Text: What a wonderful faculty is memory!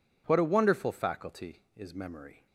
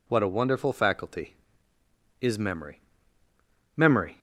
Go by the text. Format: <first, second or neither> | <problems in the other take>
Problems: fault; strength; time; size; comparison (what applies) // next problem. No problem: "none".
first | says "memory" twice; at 3.7 s